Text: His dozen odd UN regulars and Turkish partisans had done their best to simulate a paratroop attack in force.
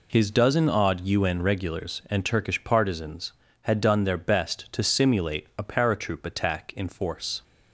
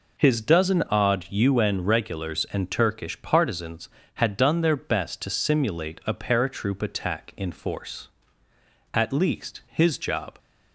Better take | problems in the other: first | goes on to say "At least his job"; from 8.9 s on; 1.4 s long

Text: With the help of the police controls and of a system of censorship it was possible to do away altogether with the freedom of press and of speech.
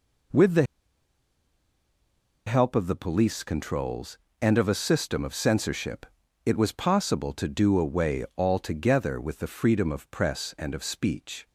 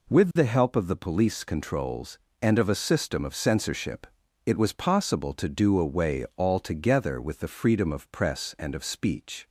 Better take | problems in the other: second | pauses between "the" and "help"; strong; at 0.6 s; 1.8 s long // pauses between "censorship" and "it"; at 6.0 s; 0.38 s long; also in the second

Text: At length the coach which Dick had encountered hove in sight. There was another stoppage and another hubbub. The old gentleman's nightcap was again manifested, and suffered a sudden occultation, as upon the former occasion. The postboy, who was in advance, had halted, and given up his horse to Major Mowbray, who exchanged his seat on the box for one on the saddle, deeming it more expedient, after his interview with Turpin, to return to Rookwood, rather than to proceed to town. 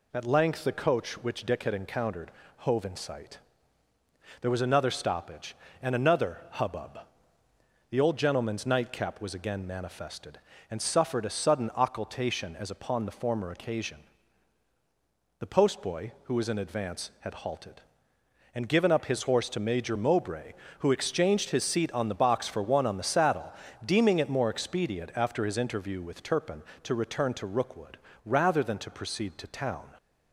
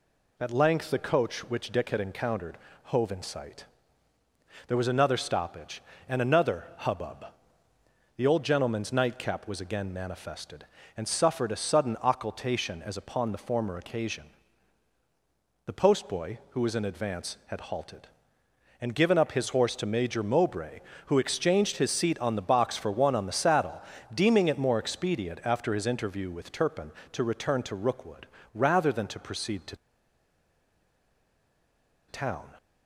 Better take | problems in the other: first | pauses between "encountered" and "hove"; slight; at 2.5 s; 0.28 s long; slight in the first // pauses between "to" and "town"; strong; at 29.7 s; 2.3 s long

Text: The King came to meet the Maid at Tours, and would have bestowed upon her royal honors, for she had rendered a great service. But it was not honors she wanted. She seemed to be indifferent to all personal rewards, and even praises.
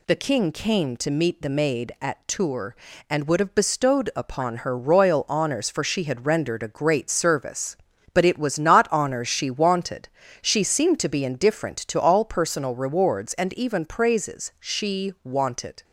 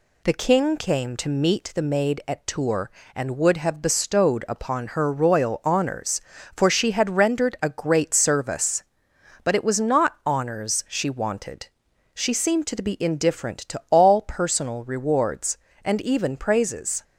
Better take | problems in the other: second | goes on to say "She wanted"; noticeable; from 14.5 s on; 1.2 s long

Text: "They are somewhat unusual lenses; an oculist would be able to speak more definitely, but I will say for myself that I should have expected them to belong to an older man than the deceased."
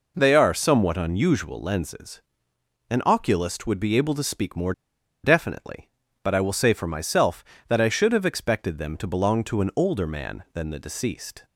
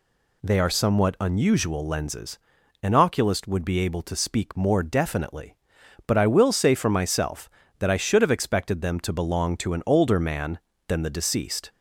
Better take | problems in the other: second | pauses between "more" and "definitely"; noticeable; at 4.7 s; 0.52 s long

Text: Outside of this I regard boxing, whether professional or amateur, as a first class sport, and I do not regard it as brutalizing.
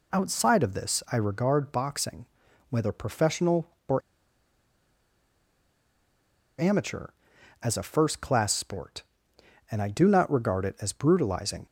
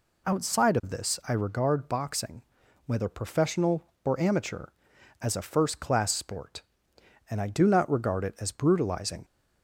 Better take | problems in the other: second | pauses between "or" and "amateur"; strong; at 4.0 s; 2.5 s long

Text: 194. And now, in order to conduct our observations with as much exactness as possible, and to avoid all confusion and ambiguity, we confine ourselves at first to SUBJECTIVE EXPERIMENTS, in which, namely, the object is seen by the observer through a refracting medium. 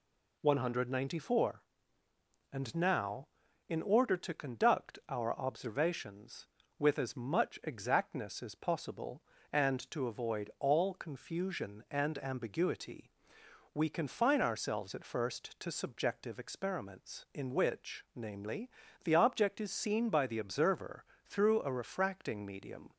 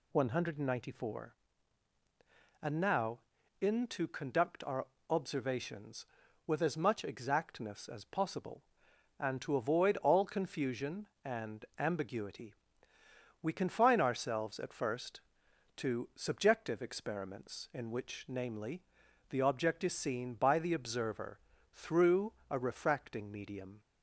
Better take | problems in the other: first | skips "order"; at 3.8 s // pauses between "our" and "observations"; slight; at 4.8 s; 0.22 s long // pauses between "observer" and "through"; slight; at 21.3 s; 0.32 s long; slight in the first // pauses between "through" and "a"; slight; at 22.3 s; 0.16 s long

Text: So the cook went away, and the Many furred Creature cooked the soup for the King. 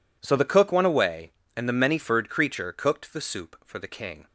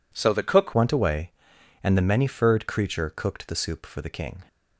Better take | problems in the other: first | changes voice at "went"; from 0.7 s on; 3.7 s long

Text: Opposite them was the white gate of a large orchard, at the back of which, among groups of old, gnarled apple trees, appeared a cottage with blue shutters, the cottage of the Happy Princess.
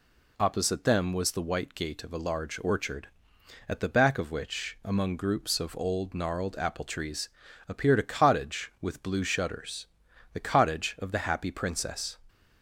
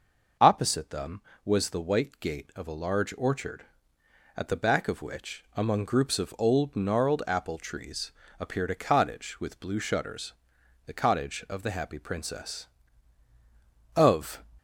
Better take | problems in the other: first | goes on to say "Of"; slight; from 13.9 s on; 0.48 s long

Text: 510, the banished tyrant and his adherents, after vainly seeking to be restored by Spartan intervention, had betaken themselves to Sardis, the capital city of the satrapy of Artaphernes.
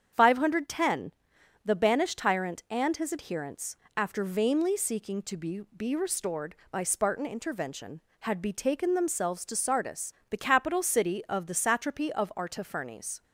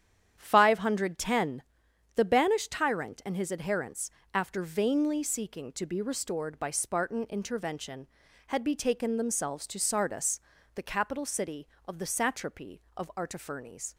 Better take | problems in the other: second | starts louder than the rest; strong; until 1.6 s; 8 dB; strong in the second // says "be" twice; at 5.7 s

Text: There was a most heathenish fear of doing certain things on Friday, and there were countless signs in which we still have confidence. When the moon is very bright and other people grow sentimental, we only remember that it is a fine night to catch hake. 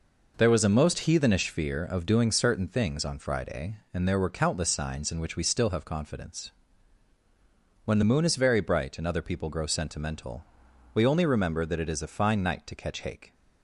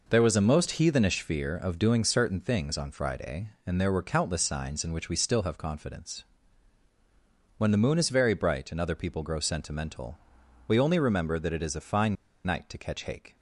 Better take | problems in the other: first | pauses between "fine" and "night"; slight; at 12.1 s; 0.30 s long

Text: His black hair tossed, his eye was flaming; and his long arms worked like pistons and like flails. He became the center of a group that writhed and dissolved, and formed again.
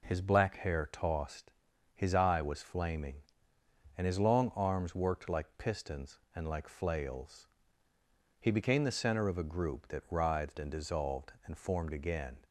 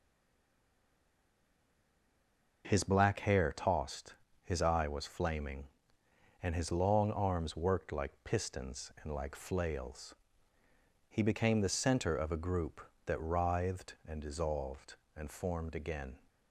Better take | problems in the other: first | stays silent before the first word; strong; until 2.6 s; 2.6 s long

